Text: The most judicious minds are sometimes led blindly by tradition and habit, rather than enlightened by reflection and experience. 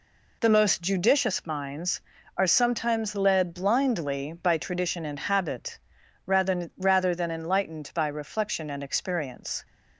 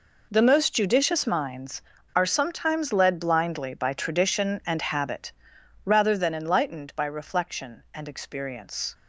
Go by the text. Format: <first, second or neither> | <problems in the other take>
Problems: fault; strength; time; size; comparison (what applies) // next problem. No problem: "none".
second | says "rather" twice; at 6.7 s